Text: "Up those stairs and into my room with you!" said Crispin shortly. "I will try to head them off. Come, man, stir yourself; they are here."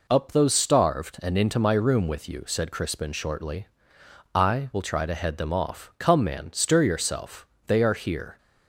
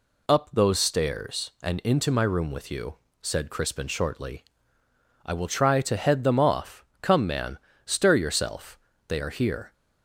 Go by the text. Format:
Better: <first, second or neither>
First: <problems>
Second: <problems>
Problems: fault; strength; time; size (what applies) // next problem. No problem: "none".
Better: second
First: says "starved" for "stairs"; at 0.5 s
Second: none